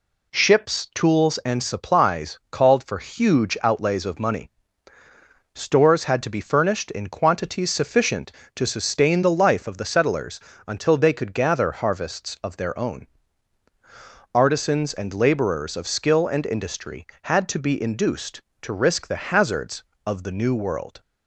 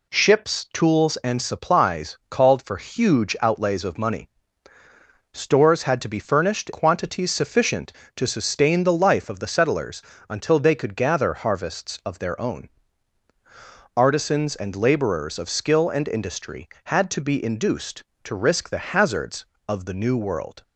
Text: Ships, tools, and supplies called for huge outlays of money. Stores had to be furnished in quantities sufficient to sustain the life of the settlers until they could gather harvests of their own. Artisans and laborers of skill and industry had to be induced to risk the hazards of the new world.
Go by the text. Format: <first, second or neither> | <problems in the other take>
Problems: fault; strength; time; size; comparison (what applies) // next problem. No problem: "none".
first | skips "in"; at 6.7 s // pauses between "settlers" and "until"; slight; at 10.0 s; 0.28 s long; slight in the first